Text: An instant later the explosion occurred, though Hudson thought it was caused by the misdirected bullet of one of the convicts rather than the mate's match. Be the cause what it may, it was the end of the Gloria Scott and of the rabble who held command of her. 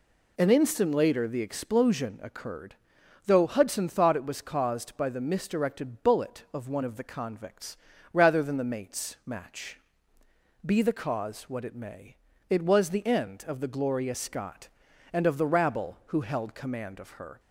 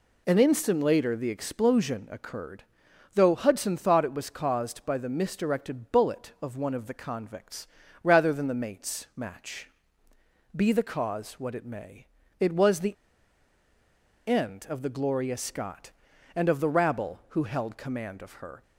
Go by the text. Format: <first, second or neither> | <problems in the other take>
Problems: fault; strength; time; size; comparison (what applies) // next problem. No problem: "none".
first | pauses between "convicts" and "rather"; slight; at 7.6 s; 0.36 s long; slight in the first // pauses between "the" and "end"; strong; at 12.9 s; 1.3 s long